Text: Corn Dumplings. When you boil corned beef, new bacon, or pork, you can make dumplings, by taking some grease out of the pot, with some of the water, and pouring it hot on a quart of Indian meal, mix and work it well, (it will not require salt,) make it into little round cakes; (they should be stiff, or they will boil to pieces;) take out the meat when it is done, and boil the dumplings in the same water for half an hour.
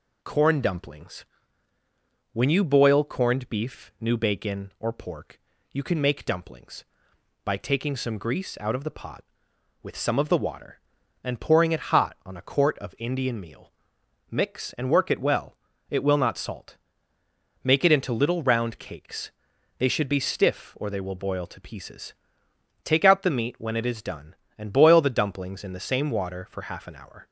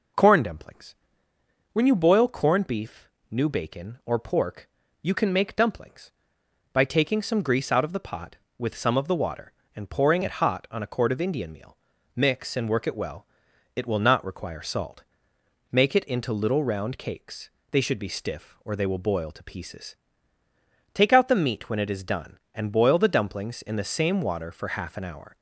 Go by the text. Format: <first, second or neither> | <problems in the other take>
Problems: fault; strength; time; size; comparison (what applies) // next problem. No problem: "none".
second | skips "require"; at 16.3 s